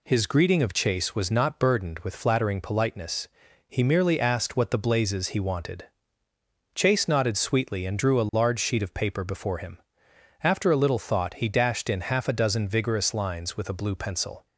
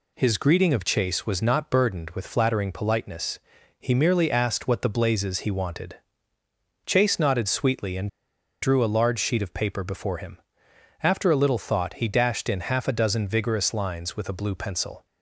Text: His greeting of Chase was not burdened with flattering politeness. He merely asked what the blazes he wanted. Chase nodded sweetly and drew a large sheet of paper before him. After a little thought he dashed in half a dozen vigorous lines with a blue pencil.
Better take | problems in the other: first | pauses between "and" and "drew"; noticeable; at 8.0 s; 0.53 s long

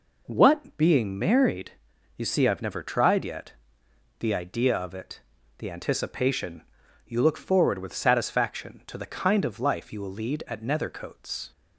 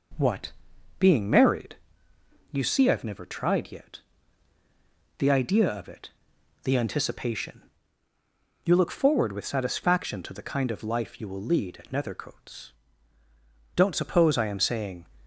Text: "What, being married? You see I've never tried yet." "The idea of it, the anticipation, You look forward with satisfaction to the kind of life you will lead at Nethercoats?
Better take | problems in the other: first | goes on to say "Don't suppose I am saying"; from 13.7 s on; 1.3 s long

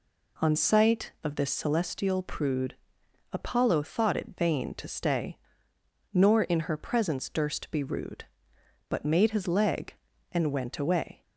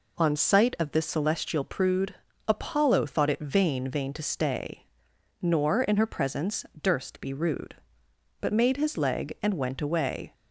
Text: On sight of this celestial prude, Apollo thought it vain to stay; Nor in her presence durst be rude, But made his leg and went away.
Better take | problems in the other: first | says "vain" twice; at 3.8 s // pauses between "presence" and "durst"; slight; at 6.6 s; 0.18 s long

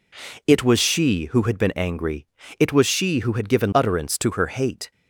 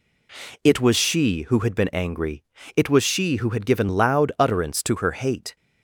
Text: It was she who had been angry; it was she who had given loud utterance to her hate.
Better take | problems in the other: second | skips "loud"; at 3.7 s

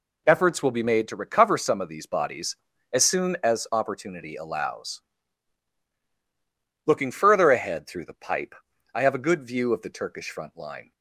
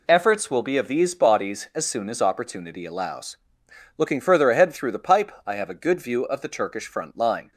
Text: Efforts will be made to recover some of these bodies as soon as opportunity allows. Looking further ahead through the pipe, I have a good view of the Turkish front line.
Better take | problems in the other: first | skips "made to recover some"; at 0.7 s

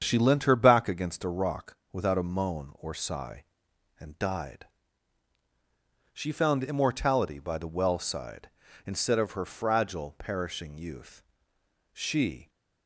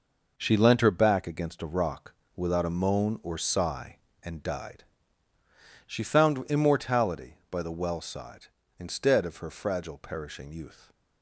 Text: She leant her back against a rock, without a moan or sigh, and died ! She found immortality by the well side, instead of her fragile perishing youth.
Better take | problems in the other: second | starts louder than the rest; strong; until 1.0 s; 7.5 dB // goes on to say "She"; from 11.9 s on; 0.56 s long

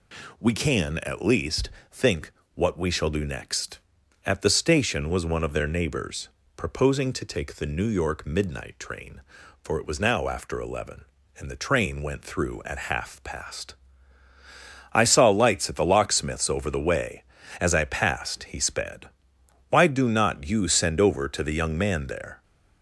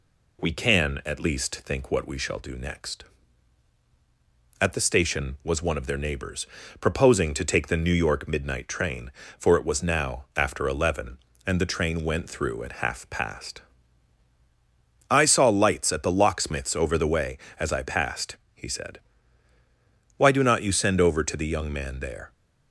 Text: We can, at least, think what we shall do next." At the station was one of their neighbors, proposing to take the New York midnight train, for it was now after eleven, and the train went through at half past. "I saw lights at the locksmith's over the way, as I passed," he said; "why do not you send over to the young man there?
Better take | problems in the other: second | pauses between "think" and "what"; slight; at 2.3 s; 0.22 s long // says "sped" for "said"; at 18.6 s

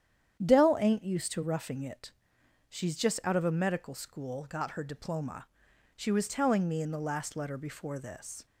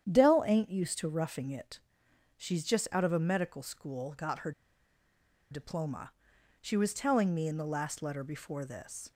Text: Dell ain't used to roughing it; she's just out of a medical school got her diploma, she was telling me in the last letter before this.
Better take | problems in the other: first | starts louder than the rest; strong; until 1.1 s; 9.5 dB; strong in the first // pauses between "her" and "diploma"; at 4.5 s; 0.98 s long

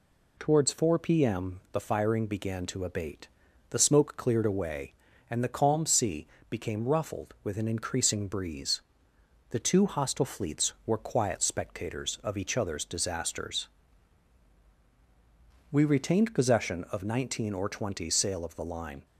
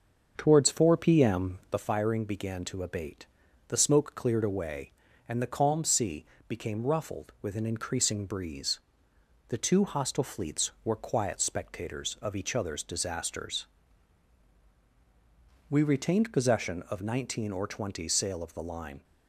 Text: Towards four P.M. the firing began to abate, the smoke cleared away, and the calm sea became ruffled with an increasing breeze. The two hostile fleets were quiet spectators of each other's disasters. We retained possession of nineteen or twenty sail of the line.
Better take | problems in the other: first | starts louder than the rest; until 1.9 s; 6.5 dB // pauses between "sea" and "became"; slight; at 6.2 s; 0.24 s long; slight in the first

